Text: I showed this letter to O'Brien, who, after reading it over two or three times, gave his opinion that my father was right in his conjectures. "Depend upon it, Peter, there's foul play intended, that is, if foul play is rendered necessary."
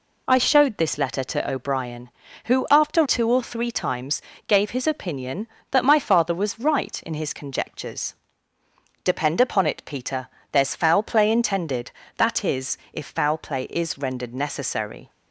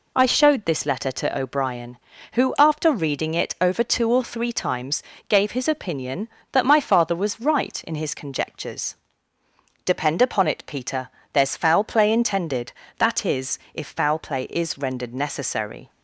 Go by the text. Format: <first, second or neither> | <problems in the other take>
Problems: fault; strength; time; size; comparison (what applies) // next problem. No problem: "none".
second | skips "reading it over"; at 3.0 s